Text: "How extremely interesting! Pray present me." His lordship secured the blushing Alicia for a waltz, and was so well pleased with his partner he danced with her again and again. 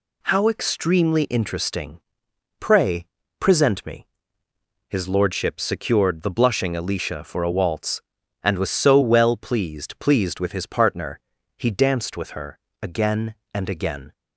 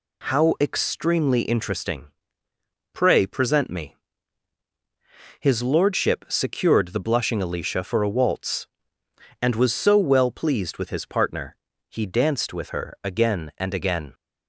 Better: second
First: pauses between "Pray" and "present"; slight; at 3.0 s; 0.32 s long // says "pleased" twice; at 10.0 s // pauses between "partner" and "he"; slight; at 11.2 s; 0.36 s long // pauses between "her" and "again"; slight; at 12.5 s; 0.24 s long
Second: pauses between "partner" and "he"; slight; at 11.5 s; 0.34 s long

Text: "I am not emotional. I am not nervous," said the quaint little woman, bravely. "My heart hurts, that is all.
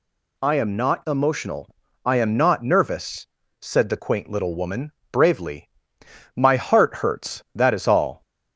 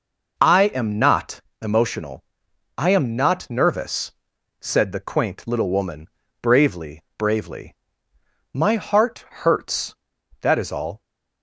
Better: first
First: none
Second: pauses between "not" and "emotional"; slight; at 1.4 s; 0.22 s long // says "bravely" twice; at 7.1 s

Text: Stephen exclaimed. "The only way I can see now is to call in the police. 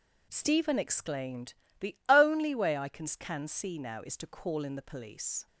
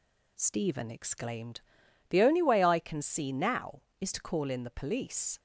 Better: second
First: says "can" twice; at 3.1 s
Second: none

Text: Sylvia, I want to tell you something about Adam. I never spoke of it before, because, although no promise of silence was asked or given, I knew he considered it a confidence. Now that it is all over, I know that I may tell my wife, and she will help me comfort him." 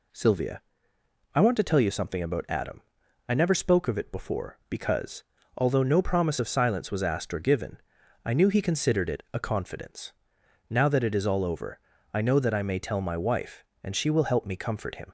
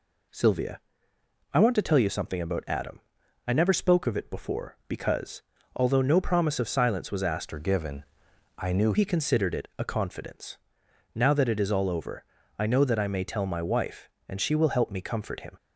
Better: first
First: none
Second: changes voice from "or" to "knew"; from 7.5 to 8.9 s; 1.4 s long

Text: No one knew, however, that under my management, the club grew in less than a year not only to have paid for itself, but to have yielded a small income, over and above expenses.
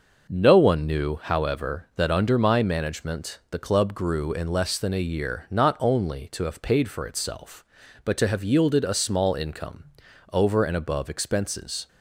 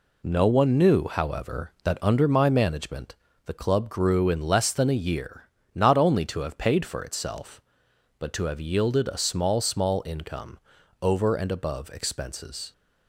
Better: first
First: none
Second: pauses between "year" and "not"; slight; at 5.4 s; 0.26 s long // says "small" twice; at 9.6 s

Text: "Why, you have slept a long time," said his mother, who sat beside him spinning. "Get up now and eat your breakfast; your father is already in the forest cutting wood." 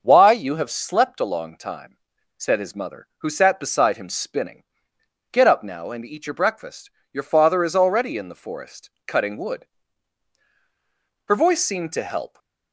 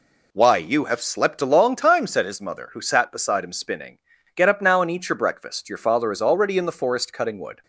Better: second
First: starts louder than the rest; until 1.0 s; 6.5 dB // pauses between "forest" and "cutting"; slight; at 8.9 s; 0.18 s long // goes on to say "Her voice seemed to help"; noticeable; from 11.2 s on; 1.1 s long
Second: none

